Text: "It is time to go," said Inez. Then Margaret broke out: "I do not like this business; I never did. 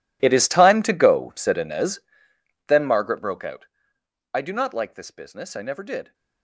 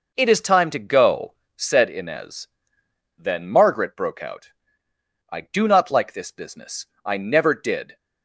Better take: second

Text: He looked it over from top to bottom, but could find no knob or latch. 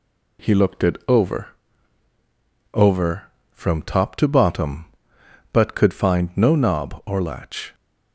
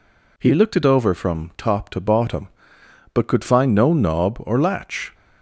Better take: second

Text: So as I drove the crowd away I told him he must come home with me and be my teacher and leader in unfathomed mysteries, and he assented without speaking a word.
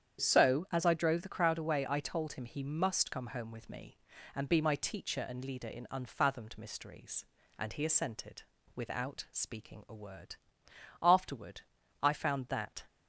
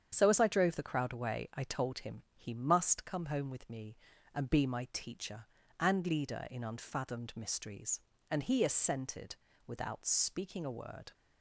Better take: second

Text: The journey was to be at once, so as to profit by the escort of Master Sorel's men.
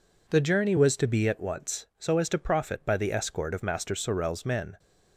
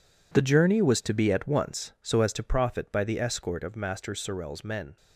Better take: first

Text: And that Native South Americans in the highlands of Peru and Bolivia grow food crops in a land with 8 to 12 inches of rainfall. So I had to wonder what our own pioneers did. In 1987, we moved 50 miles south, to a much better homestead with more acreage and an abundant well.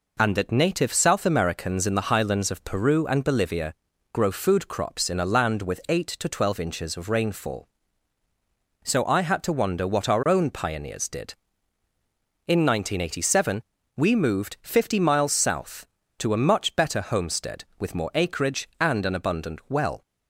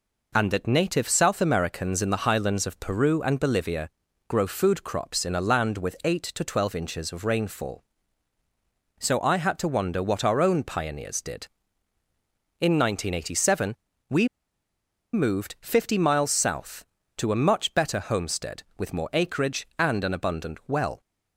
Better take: first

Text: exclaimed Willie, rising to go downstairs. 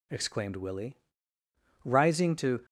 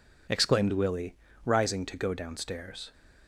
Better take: second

